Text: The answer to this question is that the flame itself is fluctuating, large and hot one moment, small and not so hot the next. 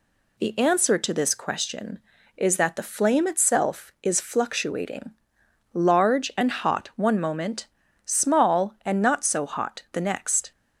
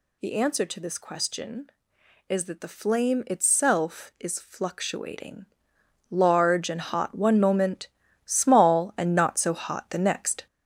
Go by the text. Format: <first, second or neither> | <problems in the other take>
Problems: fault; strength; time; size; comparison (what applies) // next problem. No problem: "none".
first | gets louder; noticeable; throughout; 5 dB